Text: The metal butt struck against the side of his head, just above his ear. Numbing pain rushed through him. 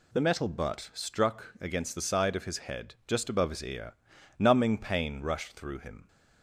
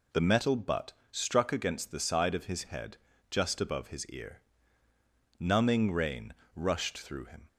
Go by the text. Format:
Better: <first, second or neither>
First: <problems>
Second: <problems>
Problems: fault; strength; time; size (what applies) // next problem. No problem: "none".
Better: first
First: none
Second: pauses between "butt" and "struck"; slight; at 0.9 s; 0.18 s long // says "rain" for "pain"; at 5.9 s